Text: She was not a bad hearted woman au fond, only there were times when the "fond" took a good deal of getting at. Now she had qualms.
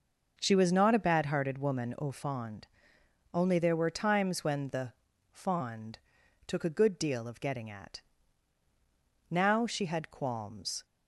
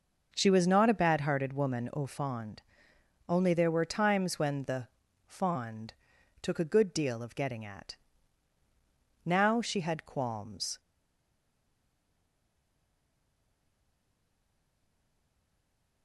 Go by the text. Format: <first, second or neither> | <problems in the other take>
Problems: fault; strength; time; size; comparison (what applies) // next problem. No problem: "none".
first | pauses between "the" and "fond"; at 4.8 s; 0.38 s long; also in the first // pauses between "fond" and "took"; noticeable; at 5.9 s; 0.48 s long; noticeable in the first // stays silent after the last word; strong; from 10.7 s on; 5.3 s long